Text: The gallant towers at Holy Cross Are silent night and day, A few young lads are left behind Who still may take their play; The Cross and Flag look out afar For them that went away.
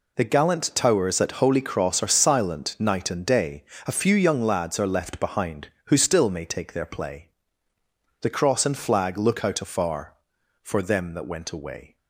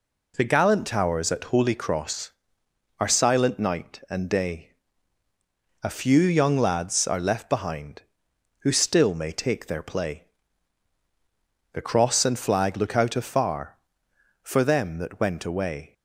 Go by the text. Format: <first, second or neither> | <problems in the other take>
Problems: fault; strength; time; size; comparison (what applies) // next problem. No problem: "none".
neither | none